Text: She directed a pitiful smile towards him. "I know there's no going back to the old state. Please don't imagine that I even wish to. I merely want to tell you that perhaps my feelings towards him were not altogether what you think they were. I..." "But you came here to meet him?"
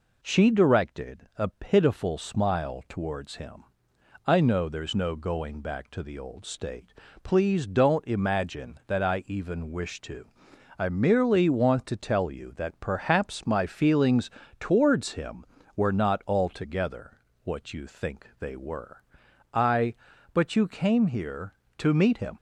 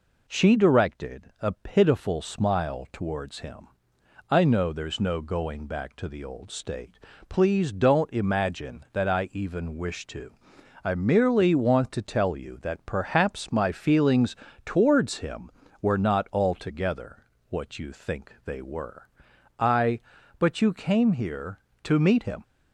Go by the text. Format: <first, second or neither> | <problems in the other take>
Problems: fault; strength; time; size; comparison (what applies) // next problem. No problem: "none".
neither | pauses between "feelings" and "towards"; slight; the same in both // pauses between "altogether" and "what"; slight; the same in both